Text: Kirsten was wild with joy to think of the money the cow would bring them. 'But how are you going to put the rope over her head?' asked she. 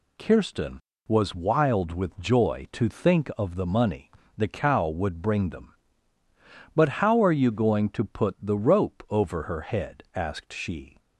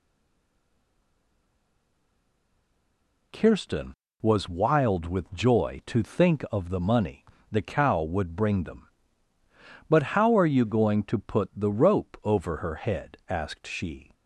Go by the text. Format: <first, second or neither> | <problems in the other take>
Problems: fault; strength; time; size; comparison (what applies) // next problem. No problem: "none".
first | stays silent before the first word; strong; until 3.3 s; 3.3 s long // pauses between "money" and "the"; slight; at 7.2 s; 0.26 s long; slight in the first